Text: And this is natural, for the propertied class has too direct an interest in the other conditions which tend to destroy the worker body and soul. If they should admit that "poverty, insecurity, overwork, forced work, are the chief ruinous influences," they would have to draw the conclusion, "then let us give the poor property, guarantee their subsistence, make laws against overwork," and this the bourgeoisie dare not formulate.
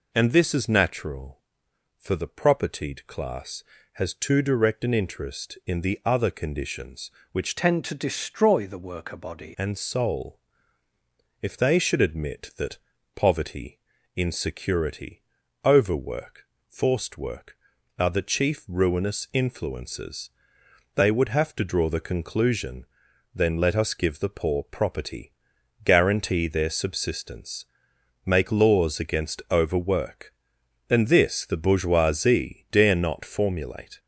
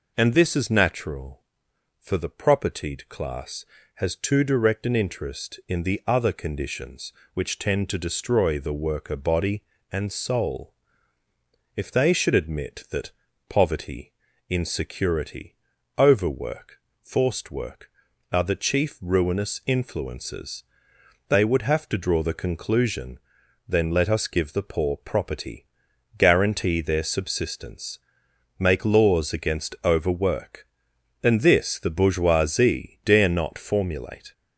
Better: second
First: changes voice from "tend" to "body"; from 7.5 to 9.5 s; 2.0 s long // pauses between "that" and "poverty"; slight; at 12.7 s; 0.36 s long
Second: pauses between "that" and "poverty"; slight; at 13.1 s; 0.36 s long

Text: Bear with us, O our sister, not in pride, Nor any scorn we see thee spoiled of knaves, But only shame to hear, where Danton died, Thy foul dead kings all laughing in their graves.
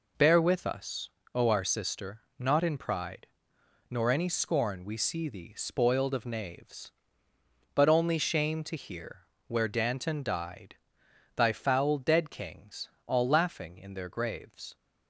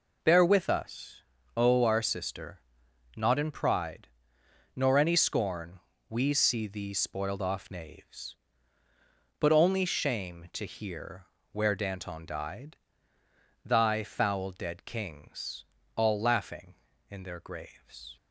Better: first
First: pauses between "kings" and "all"; slight; at 12.8 s; 0.20 s long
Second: pauses between "scorn" and "we"; slight; at 5.8 s; 0.30 s long // says "off" for "of"; at 7.4 s // pauses between "kings" and "all"; slight; at 15.6 s; 0.32 s long

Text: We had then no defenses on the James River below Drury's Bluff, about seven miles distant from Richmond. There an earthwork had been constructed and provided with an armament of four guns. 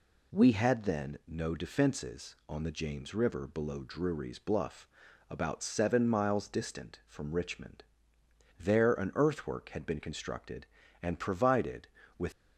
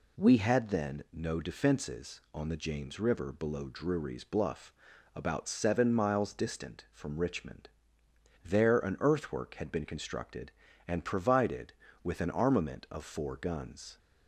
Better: second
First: stops before "an armament of four guns"; at 12.3 s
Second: none

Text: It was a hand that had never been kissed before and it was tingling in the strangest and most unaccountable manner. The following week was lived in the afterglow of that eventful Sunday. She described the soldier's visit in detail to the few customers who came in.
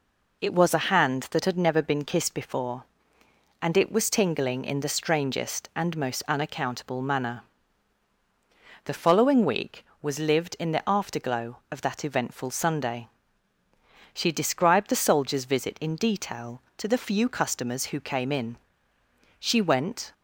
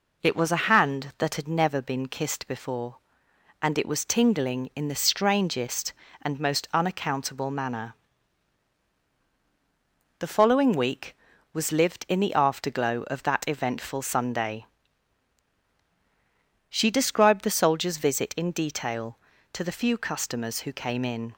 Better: second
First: goes on to say "She went"; noticeable; from 19.3 s on; 0.74 s long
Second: none

